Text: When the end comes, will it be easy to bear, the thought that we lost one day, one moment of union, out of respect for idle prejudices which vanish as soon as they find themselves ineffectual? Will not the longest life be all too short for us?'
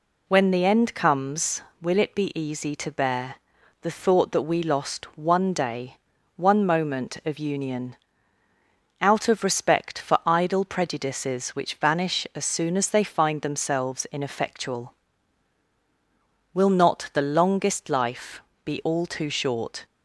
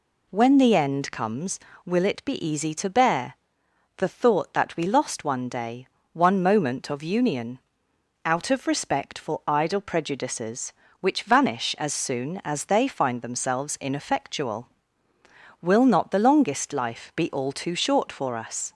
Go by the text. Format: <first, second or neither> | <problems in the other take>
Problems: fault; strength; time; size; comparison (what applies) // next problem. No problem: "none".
second | pauses between "life" and "be"; slight; at 18.4 s; 0.24 s long // stops before "for us"; at 19.8 s